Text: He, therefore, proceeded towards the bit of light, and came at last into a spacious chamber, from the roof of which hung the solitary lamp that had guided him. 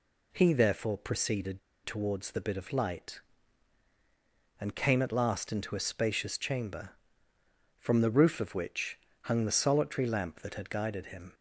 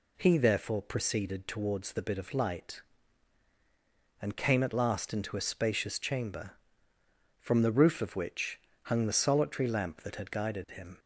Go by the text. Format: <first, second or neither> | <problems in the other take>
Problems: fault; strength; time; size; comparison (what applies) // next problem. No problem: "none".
second | pauses between "proceeded" and "towards"; slight; at 1.6 s; 0.25 s long // pauses between "which" and "hung"; slight; at 8.9 s; 0.24 s long; slight in the second